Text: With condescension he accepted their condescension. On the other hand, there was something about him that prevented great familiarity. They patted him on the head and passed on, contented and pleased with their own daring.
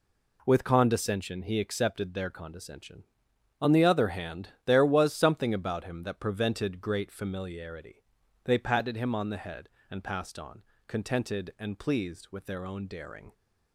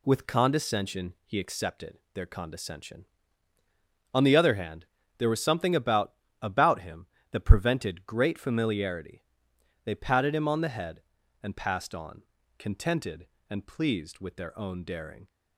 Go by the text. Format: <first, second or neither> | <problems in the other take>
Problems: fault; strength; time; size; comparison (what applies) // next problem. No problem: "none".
first | pauses between "accepted" and "their"; slight; at 1.9 s; 0.16 s long // says "about" twice; at 6.4 s